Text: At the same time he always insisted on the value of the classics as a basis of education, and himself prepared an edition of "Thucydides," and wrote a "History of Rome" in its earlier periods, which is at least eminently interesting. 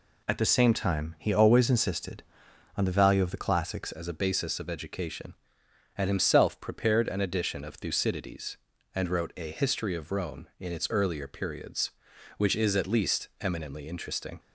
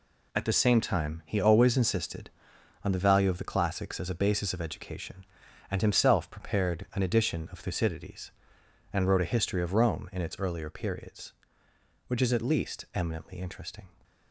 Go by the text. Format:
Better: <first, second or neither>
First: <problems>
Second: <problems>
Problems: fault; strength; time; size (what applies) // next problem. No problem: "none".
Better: second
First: changes voice at "as"; from 3.9 s on; 10.4 s long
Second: none